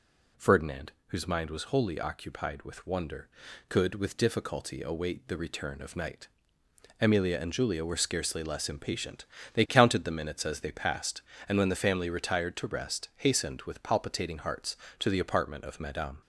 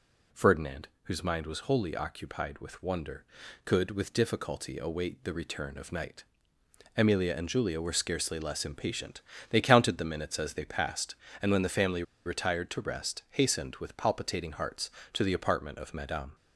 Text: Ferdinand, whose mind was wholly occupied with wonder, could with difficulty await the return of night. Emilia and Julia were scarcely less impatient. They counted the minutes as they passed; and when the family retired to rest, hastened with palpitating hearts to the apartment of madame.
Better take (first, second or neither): first